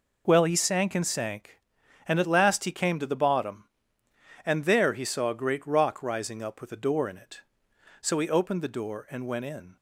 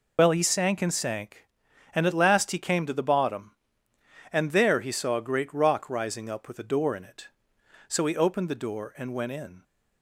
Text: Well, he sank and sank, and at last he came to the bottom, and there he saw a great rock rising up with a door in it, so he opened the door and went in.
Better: first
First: none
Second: loses the start of "Well"; at 0.1 s; 70 ms

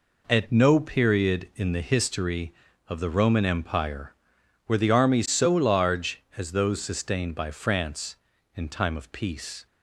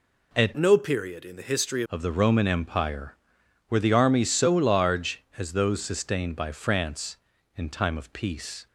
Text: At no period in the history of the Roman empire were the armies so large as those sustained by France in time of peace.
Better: first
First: none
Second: changes voice from "no" to "history"; from 0.5 to 1.8 s; 1.3 s long

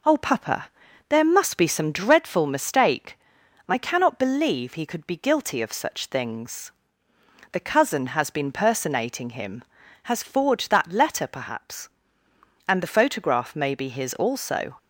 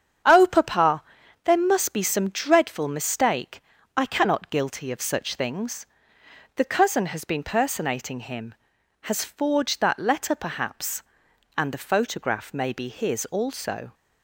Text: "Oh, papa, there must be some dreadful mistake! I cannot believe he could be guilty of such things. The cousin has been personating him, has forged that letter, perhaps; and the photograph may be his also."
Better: first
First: none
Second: starts louder than the rest; strong; until 1.6 s; 8 dB // skips "believe he could be"; at 4.4 s

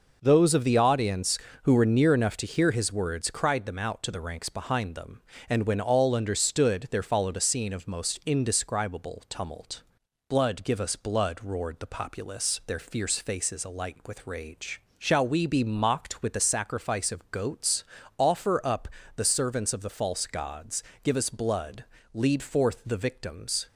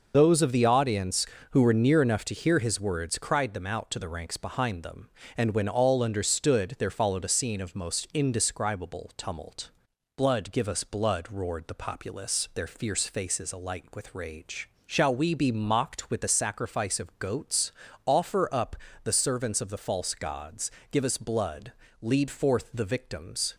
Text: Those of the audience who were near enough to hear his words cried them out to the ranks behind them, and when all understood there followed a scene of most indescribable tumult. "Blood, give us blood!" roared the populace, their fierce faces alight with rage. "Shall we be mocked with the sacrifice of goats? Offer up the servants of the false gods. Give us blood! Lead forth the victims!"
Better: first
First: pauses between "up" and "the"; slight; at 18.8 s; 0.30 s long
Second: loses the start of "Those"; at 0.1 s; 50 ms // pauses between "up" and "the"; slight; at 18.7 s; 0.30 s long

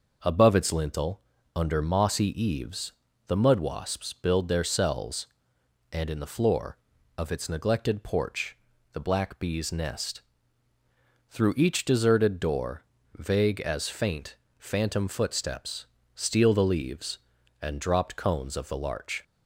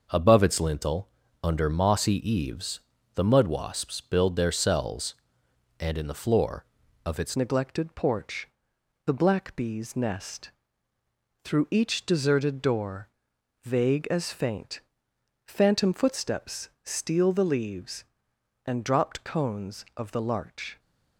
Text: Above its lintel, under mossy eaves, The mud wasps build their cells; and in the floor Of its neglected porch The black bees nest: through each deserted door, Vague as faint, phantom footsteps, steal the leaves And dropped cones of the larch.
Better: first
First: pauses between "porch" and "The"; slight; at 8.5 s; 0.34 s long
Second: changes voice at "neglected"; from 7.3 s on; 13.4 s long // pauses between "porch" and "The"; noticeable; at 8.4 s; 0.56 s long

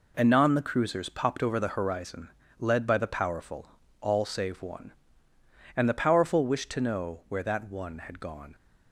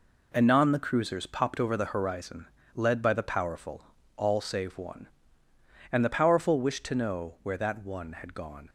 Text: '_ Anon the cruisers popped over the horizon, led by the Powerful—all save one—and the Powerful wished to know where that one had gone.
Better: neither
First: none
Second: none

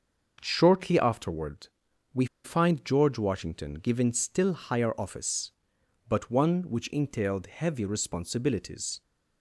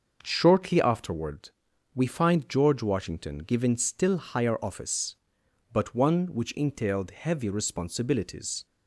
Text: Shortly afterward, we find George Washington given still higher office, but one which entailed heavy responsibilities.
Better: second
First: starts louder than the rest; until 1.4 s; 6.5 dB // pauses between "we" and "find"; slight; at 2.2 s; 0.19 s long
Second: starts louder than the rest; until 1.2 s; 6.5 dB

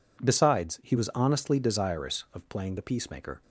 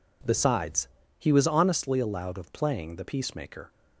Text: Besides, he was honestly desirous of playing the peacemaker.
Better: first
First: none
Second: says "allowed" for "desirous"; at 1.9 s

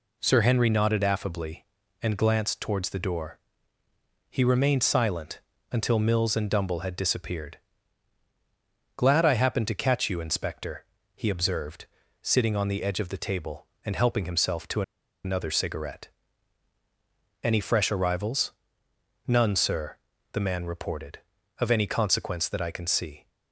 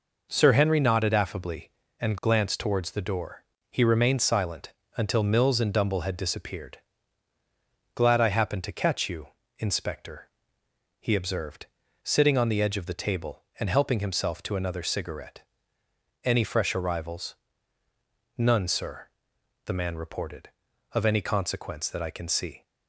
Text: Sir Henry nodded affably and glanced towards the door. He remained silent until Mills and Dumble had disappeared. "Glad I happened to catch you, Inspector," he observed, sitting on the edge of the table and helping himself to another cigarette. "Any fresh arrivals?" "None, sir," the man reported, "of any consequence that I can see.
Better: second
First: pauses between "silent" and "until"; slight; at 5.4 s; 0.30 s long // pauses between "to" and "another"; at 14.8 s; 0.42 s long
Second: pauses between "silent" and "until"; slight; at 4.7 s; 0.24 s long

